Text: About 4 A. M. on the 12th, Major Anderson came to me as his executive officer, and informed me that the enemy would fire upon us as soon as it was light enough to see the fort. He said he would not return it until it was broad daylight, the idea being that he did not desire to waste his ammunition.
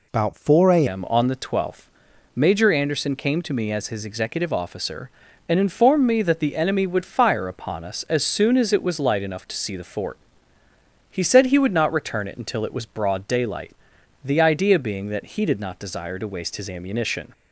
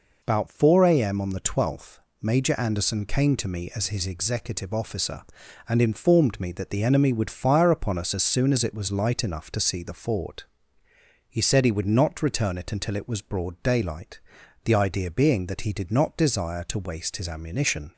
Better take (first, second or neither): second